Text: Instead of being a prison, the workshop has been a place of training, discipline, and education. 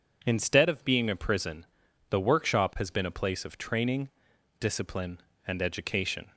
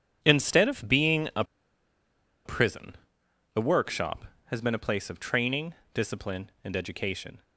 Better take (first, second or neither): first